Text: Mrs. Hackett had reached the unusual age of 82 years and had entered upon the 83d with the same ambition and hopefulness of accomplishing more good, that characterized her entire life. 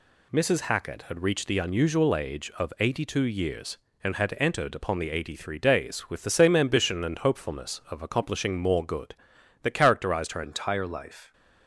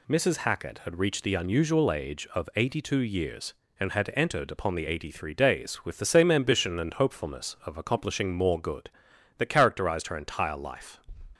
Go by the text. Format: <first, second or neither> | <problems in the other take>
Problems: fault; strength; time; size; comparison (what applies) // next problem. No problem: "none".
second | changes voice at "entire"; from 10.4 s on; 0.9 s long